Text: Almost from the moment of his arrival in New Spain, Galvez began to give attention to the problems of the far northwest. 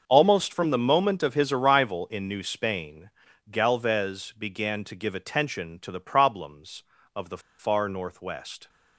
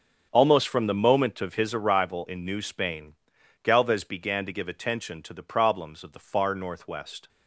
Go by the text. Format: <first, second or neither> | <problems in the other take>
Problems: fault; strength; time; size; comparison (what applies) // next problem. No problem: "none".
second | starts louder than the rest; until 1.0 s; 6.5 dB; strong in the second // pauses between "the" and "far"; slight; at 7.3 s; 0.19 s long